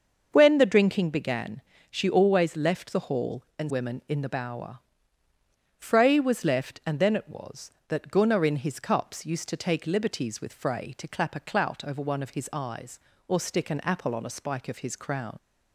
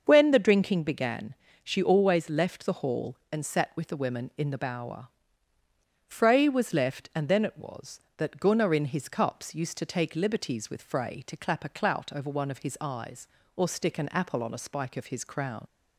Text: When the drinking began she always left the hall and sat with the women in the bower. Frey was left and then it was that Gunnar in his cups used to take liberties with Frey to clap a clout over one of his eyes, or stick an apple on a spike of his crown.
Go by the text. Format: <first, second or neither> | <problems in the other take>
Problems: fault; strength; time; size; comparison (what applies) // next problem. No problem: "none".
second | starts louder than the rest; until 1.3 s; 6.5 dB; also in the second // pauses between "began" and "she"; slight; at 1.6 s; 0.30 s long; slight in the second // skips "sat with the"; at 3.7 s